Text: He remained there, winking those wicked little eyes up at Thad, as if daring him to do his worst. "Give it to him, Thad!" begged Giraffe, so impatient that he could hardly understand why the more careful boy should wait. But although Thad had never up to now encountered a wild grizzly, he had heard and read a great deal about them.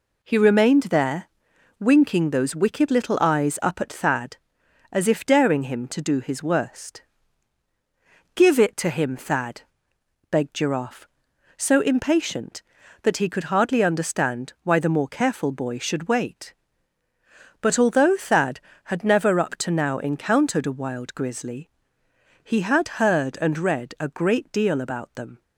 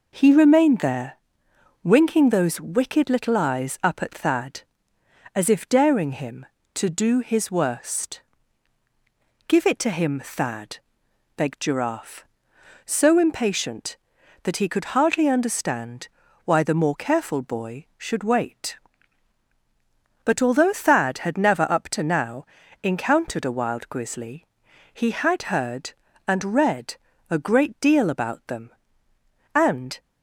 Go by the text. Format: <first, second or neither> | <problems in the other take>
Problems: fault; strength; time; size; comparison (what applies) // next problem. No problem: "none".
first | pauses between "understand" and "why"; at 16.0 s; 0.38 s long // pauses between "now" and "encountered"; at 22.4 s; 0.38 s long // pauses between "read" and "a"; slight; at 26.9 s; 0.32 s long // goes on to say "And"; slight; from 29.5 s on; 0.44 s long